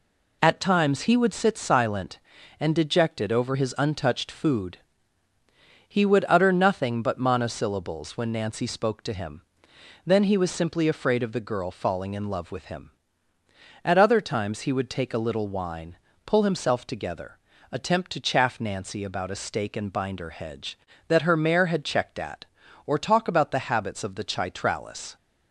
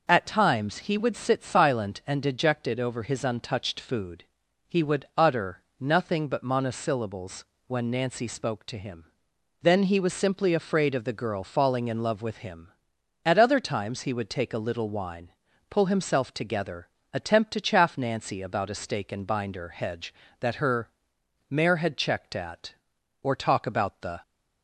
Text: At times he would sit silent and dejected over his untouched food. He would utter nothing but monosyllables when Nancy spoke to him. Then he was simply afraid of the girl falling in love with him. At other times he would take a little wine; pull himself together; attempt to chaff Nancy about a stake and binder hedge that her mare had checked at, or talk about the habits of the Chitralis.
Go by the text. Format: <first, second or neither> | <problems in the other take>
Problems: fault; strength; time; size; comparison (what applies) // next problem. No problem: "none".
first | pauses between "utter" and "nothing"; slight; at 5.6 s; 0.18 s long // pauses between "monosyllables" and "when"; slight; at 7.4 s; 0.22 s long // pauses between "her" and "mare"; noticeable; at 20.8 s; 0.62 s long // stops before "habits of the Chitralis"; at 24.2 s